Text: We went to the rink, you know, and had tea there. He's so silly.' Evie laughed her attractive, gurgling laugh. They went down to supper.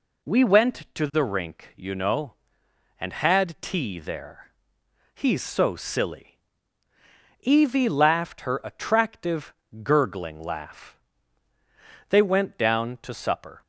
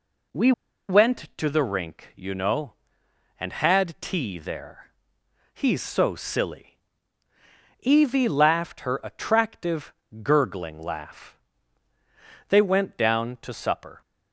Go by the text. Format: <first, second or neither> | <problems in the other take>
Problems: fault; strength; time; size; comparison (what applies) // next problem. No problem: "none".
first | pauses between "We" and "went"; at 0.5 s; 0.36 s long